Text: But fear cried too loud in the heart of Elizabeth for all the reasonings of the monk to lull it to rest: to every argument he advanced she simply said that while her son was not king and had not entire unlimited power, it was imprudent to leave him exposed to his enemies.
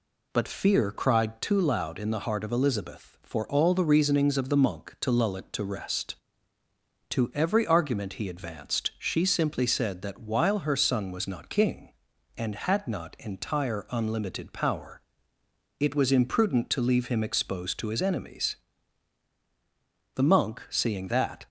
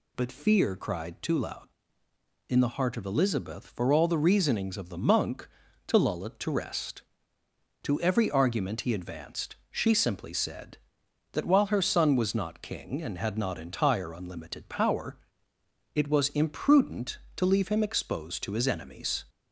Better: second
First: goes on to say "The monk seeing that"; from 20.1 s on; 1.3 s long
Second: none

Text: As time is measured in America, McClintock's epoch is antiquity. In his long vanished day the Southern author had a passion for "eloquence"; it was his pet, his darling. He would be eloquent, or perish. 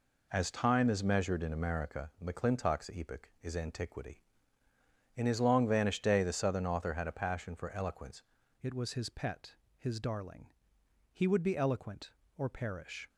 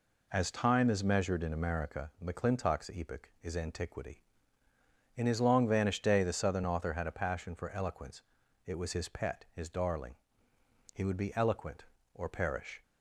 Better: second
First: changes voice at "it"; from 8.6 s on; 4.4 s long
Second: none

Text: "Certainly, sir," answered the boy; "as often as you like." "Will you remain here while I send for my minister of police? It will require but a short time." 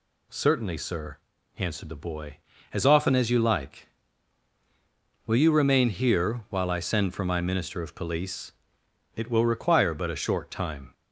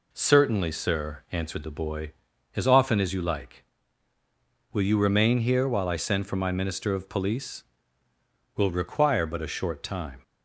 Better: first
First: none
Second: skips "It"; at 8.0 s

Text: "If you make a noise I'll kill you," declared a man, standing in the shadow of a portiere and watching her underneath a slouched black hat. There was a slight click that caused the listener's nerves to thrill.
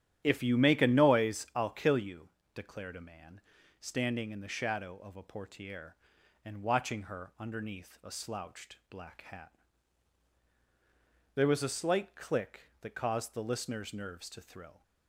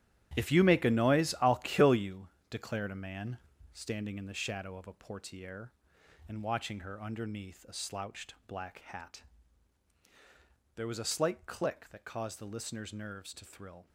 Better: first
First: starts louder than the rest; strong; until 1.2 s; 10.5 dB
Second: gets quieter; strong; throughout; 11.5 dB // starts louder than the rest; strong; until 1.4 s; 11.5 dB

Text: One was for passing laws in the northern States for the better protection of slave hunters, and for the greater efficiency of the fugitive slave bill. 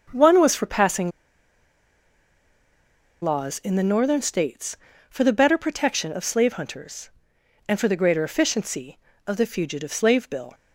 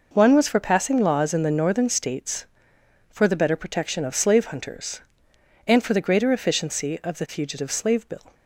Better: second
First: starts louder than the rest; until 3.2 s; 6.5 dB // pauses between "passing" and "laws"; strong; at 1.1 s; 2.1 s long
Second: none

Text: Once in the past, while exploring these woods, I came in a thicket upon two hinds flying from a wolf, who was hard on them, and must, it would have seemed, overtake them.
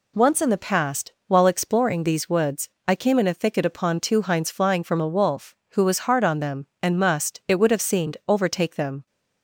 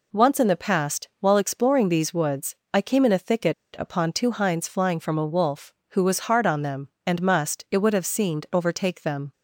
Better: first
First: none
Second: pauses between "thicket" and "upon"; slight; at 3.5 s; 0.25 s long

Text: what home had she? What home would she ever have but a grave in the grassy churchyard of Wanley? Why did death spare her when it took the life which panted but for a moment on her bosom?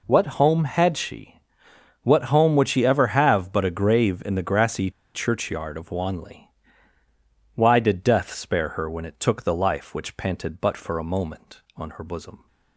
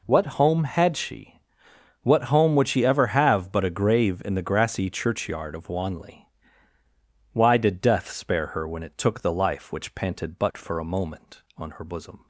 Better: second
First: pauses between "grassy" and "churchyard"; slight; at 4.9 s; 0.23 s long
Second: none

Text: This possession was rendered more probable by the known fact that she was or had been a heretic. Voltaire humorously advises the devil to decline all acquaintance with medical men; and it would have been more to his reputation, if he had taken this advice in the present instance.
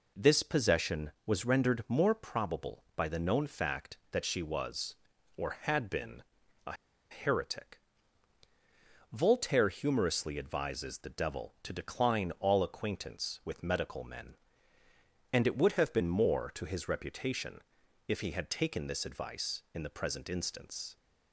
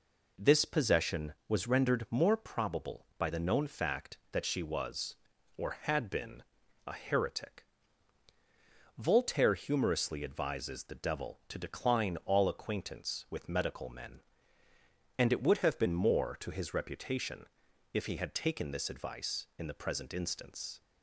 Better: second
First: pauses between "been" and "a"; at 6.2 s; 0.44 s long // pauses between "a" and "heretic"; at 6.7 s; 0.37 s long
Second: pauses between "been" and "a"; at 6.4 s; 0.44 s long

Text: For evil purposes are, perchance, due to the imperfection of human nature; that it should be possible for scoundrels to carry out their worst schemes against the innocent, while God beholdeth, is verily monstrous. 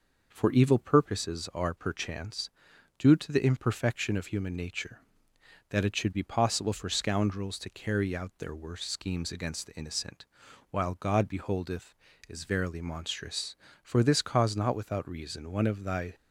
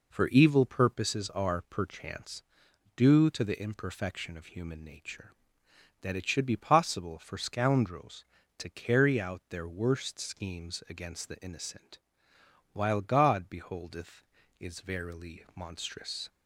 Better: second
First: goes on to say "For this cause not without reason one of thy"; strong; from 13.8 s on; 2.3 s long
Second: none

